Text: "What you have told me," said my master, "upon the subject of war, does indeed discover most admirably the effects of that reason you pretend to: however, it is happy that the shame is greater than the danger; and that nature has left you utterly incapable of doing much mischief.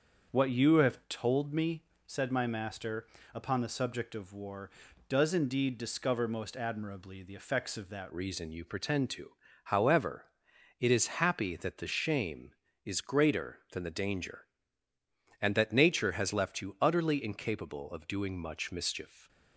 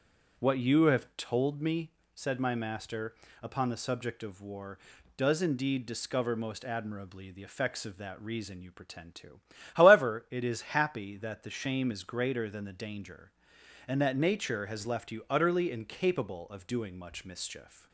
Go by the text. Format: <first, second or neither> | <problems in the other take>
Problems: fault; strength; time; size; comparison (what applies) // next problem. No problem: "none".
second | starts louder than the rest; until 1.4 s; 7 dB; strong in the second // changes voice at "reason"; from 8.0 s on; 11.2 s long